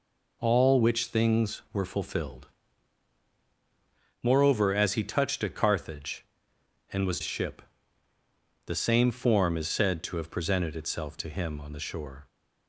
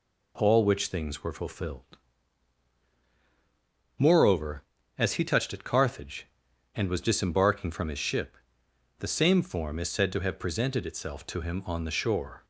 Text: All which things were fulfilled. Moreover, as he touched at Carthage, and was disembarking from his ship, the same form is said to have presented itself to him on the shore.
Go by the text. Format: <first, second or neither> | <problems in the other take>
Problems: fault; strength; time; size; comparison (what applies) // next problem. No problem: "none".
second | skips "disembarking from his"; at 7.2 s